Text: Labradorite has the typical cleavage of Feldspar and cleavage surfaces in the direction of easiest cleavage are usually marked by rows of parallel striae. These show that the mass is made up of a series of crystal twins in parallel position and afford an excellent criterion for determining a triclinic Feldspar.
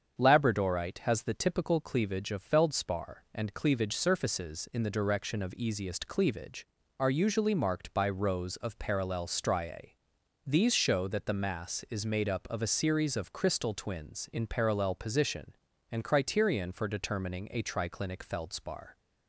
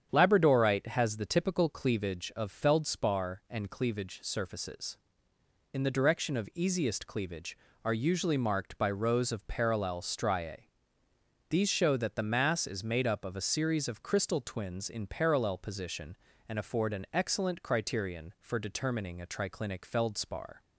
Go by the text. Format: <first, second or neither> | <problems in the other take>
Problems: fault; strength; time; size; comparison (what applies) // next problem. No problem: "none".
second | starts louder than the rest; strong; until 1.2 s; 7.5 dB; strong in the second // skips "afford an excellent"; at 16.0 s